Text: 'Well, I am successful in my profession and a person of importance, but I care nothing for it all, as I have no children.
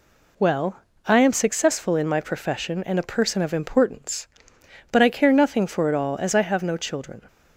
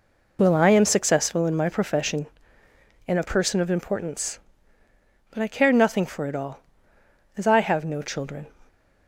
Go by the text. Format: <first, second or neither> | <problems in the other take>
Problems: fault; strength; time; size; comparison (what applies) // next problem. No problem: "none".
neither | none